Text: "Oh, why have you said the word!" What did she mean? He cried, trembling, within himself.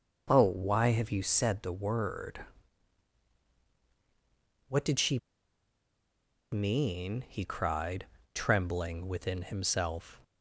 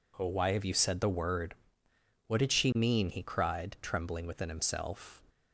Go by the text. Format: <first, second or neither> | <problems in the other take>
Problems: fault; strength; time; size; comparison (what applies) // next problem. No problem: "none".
second | pauses between "she" and "mean"; strong; at 5.1 s; 1.3 s long